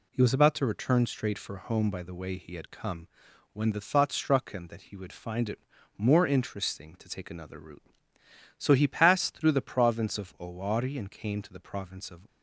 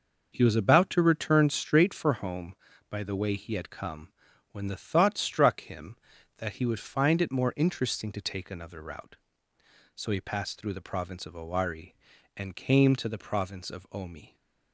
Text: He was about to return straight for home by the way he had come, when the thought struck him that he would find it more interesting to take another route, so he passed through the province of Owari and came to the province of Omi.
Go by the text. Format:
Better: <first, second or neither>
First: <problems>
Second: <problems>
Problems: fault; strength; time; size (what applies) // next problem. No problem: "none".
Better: second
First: pauses between "it" and "more"; at 5.5 s; 0.38 s long // stops before "Omi"; at 12.2 s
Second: none